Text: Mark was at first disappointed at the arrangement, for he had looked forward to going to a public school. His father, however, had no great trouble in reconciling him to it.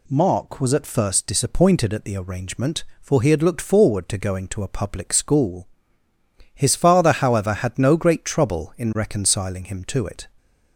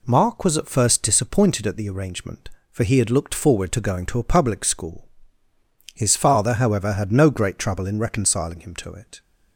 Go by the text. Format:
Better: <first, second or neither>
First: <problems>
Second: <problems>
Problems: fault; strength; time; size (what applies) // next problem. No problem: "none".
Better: neither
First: none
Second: none